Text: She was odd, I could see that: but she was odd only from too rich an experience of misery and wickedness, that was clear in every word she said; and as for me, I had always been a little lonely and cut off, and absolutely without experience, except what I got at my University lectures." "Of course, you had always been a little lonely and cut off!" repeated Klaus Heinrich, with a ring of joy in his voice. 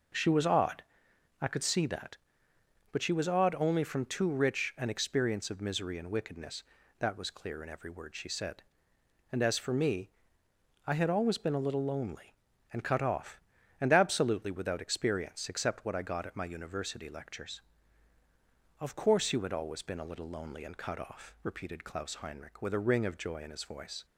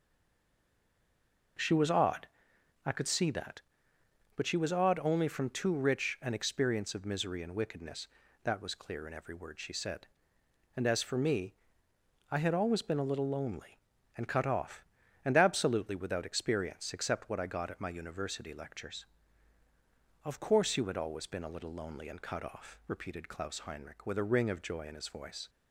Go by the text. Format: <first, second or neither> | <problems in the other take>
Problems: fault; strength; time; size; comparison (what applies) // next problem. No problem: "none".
first | stays silent before the first word; noticeable; until 1.5 s; 1.5 s long